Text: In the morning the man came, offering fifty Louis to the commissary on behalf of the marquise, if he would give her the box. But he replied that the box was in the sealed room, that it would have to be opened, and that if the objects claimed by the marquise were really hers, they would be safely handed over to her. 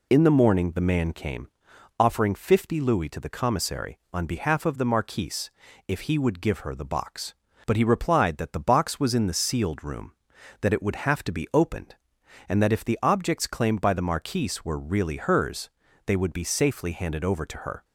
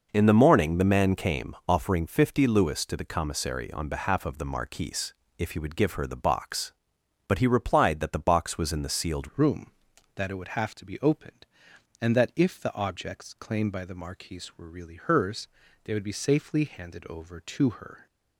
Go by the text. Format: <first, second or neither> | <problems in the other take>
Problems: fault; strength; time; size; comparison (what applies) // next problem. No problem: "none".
first | changes voice at "room"; from 9.3 s on; 8.7 s long